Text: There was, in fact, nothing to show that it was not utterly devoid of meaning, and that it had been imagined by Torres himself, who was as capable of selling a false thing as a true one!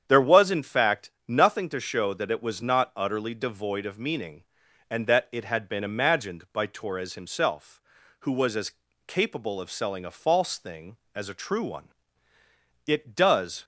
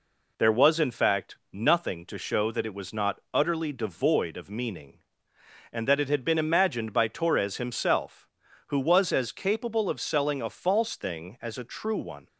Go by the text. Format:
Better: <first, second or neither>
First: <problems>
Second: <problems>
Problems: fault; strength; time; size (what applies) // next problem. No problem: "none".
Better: second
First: starts louder than the rest; strong; until 1.0 s; 8.5 dB // pauses between "as" and "capable"; slight; at 8.7 s; 0.36 s long // goes on to say "It does"; noticeable; from 12.8 s on; 0.78 s long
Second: none